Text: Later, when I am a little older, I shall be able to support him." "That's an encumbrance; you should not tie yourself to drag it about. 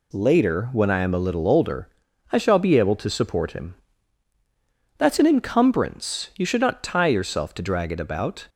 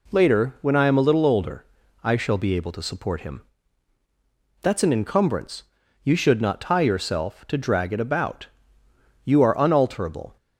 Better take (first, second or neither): first